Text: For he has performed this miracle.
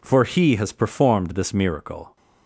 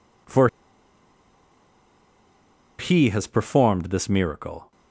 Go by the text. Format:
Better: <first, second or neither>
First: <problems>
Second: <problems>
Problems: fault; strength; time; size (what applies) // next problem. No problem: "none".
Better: first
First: none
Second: pauses between "For" and "he"; strong; at 0.4 s; 2.3 s long